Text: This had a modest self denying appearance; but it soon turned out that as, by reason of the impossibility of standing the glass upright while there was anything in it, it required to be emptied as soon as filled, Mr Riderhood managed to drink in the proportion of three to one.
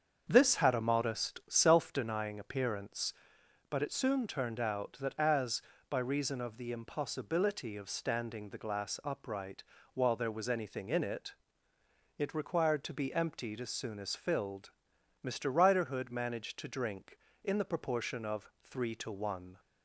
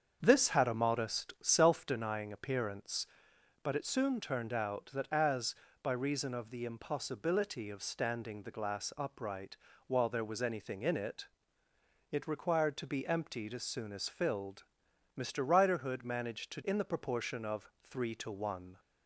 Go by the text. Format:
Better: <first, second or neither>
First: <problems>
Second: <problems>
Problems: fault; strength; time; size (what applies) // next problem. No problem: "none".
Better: first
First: starts louder than the rest; strong; until 1.2 s; 7 dB // pauses between "upright" and "while"; slight; at 9.6 s; 0.30 s long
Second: starts louder than the rest; strong; until 1.2 s; 7 dB // pauses between "upright" and "while"; slight; at 9.5 s; 0.30 s long // skips "drink"; at 16.6 s